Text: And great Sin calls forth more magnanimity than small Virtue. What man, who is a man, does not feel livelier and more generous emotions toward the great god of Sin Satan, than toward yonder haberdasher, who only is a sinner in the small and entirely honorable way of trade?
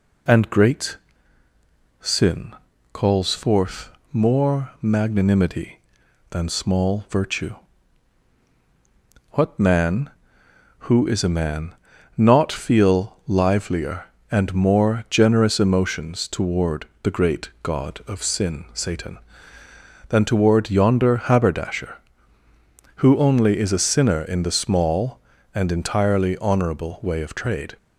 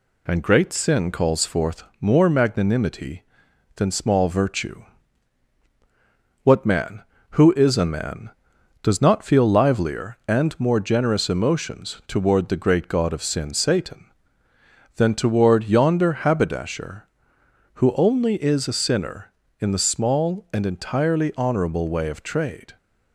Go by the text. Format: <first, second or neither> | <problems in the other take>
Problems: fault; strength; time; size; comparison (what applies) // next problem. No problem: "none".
second | pauses between "great" and "Sin"; at 0.9 s; 1.0 s long // pauses between "Sin" and "calls"; at 2.5 s; 0.38 s long // pauses between "forth" and "more"; slight; at 3.9 s; 0.20 s long; slight in the second // skips "does"; at 11.9 s // pauses between "toward" and "the"; slight; at 16.8 s; 0.16 s long